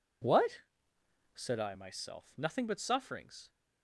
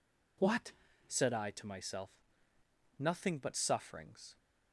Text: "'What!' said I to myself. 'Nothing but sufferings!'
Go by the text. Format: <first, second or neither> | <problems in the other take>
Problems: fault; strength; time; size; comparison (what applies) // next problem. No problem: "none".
second | skips "to"; at 1.7 s